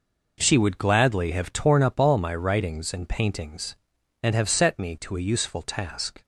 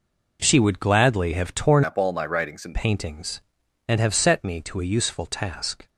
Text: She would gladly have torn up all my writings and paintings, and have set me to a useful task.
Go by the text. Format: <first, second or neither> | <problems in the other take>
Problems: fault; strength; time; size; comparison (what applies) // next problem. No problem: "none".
first | changes voice from "up" to "and"; from 1.8 to 2.7 s; 0.9 s long